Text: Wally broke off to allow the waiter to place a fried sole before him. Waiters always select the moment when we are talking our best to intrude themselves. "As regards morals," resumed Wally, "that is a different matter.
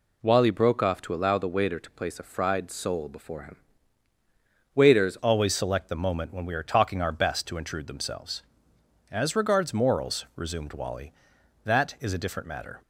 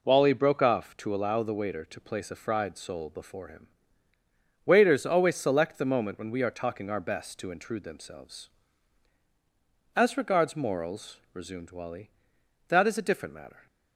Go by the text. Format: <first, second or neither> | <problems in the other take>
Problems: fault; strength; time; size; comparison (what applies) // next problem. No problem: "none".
second | changes voice at "always"; from 5.1 s on; 7.7 s long